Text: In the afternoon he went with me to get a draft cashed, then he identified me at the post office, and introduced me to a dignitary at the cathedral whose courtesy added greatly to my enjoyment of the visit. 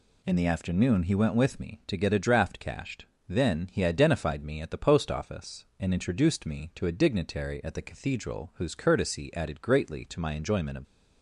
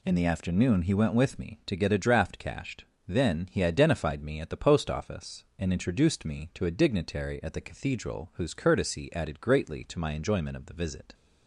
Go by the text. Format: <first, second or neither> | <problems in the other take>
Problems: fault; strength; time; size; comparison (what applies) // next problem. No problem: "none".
second | stops before "the visit"; at 10.8 s